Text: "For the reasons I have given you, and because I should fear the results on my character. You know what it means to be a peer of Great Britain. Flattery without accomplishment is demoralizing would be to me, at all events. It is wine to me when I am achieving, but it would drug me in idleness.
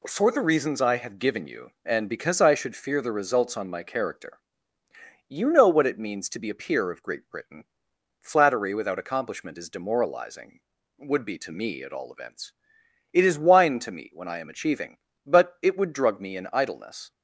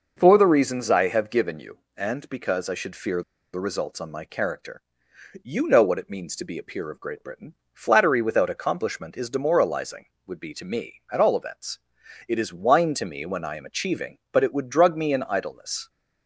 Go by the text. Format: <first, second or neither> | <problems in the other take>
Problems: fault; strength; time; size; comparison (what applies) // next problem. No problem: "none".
first | starts louder than the rest; noticeable; until 1.1 s; 6 dB // pauses between "fear" and "the"; slight; at 3.2 s; 0.31 s long